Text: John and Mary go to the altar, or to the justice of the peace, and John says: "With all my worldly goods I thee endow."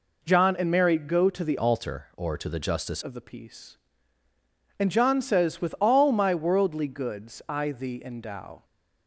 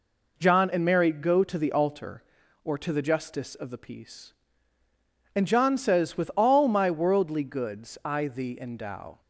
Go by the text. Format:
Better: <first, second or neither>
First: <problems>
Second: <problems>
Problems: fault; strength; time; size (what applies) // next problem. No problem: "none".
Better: second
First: changes voice from "altar" to "justice"; from 1.5 to 3.0 s; 1.5 s long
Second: none